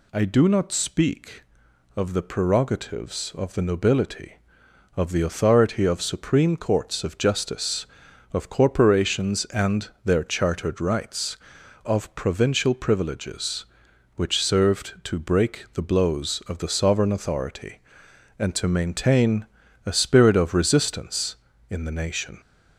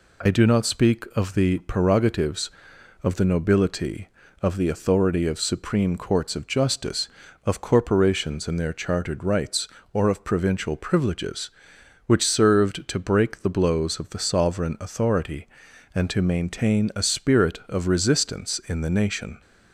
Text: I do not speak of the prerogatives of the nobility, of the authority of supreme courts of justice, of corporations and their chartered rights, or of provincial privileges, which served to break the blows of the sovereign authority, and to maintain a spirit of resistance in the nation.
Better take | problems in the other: second | pauses between "and" and "their"; slight; at 9.8 s; 0.16 s long // skips "or"; at 11.6 s // pauses between "maintain" and "a"; at 19.4 s; 0.40 s long

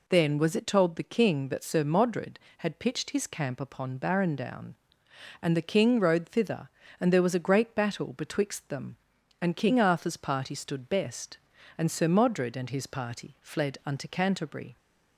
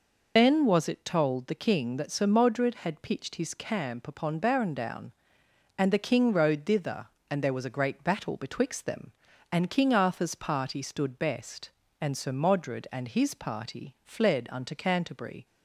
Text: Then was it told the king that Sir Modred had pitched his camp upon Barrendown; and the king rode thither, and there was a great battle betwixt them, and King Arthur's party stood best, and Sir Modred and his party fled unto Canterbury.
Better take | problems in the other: first | loses the start of "Then"; at 0.3 s; 45 ms

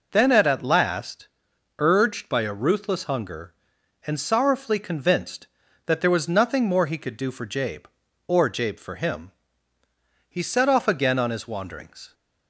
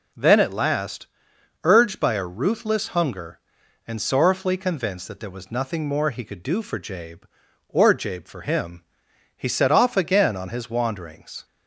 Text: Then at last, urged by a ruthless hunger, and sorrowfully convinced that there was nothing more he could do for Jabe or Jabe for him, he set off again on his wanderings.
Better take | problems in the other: second | says "at" twice; at 0.4 s

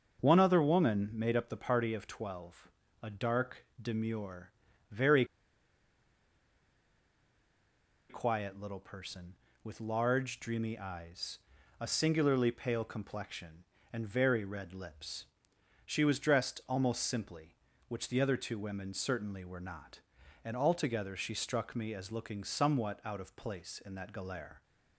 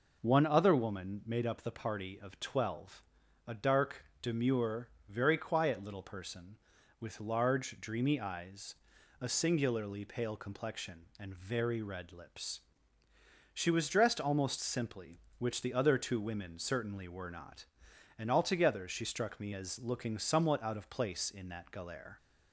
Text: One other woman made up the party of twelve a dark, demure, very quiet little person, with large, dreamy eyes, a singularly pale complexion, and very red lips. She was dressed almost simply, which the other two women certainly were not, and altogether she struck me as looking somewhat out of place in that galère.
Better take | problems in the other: second | starts louder than the rest; until 1.2 s; 6 dB // pauses between "twelve" and "a"; slight; at 2.6 s; 0.34 s long; also in the second // pauses between "very" and "quiet"; strong; at 5.2 s; 2.8 s long

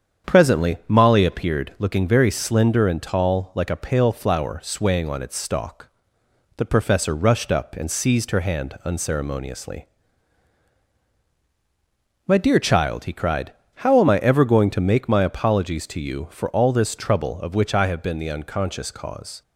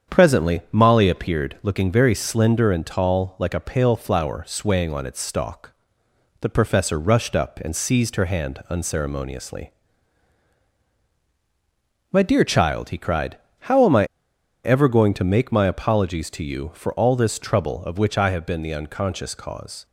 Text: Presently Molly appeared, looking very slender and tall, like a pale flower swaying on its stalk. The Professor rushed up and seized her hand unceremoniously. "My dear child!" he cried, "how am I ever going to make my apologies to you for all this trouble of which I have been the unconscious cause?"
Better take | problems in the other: first | starts louder than the rest; strong; until 1.2 s; 7.5 dB; strong in the first // pauses between "I" and "ever"; noticeable; at 14.0 s; 0.59 s long

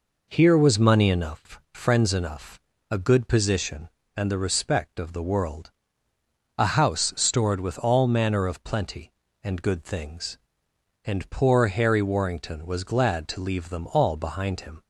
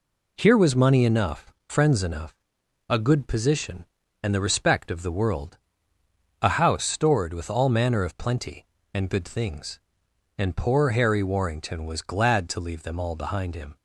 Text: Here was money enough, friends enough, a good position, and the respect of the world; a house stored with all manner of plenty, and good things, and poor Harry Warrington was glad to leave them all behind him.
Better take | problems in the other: second | starts louder than the rest; noticeable; until 1.2 s; 4.5 dB

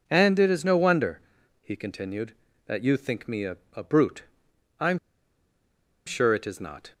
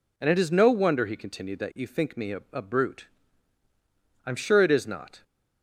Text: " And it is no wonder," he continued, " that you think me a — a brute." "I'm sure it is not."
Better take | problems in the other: second | pauses between "I'm" and "sure"; at 4.9 s; 1.0 s long

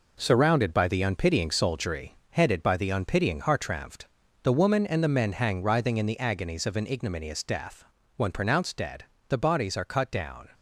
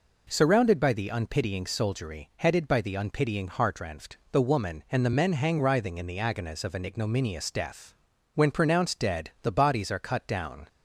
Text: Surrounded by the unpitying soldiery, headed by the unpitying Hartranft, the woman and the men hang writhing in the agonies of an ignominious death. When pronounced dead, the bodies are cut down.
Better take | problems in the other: second | gets quieter; strong; throughout; 7.5 dB

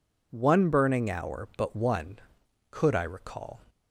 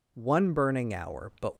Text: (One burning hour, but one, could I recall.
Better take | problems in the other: first | stops before "one could I recall"; at 1.5 s

